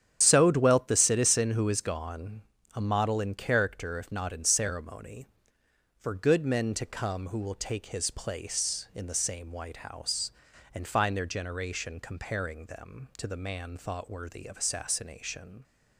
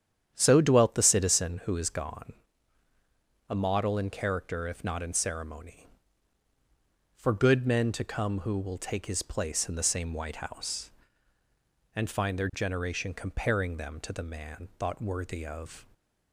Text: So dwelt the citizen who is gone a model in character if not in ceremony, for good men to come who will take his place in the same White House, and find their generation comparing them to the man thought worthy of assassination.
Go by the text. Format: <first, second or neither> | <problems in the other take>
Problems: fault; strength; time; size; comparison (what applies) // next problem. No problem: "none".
first | starts louder than the rest; strong; until 1.3 s; 9 dB; strong in the first // pauses between "gone" and "a"; at 2.3 s; 1.1 s long; slight in the first // stops before "assassination"; at 15.9 s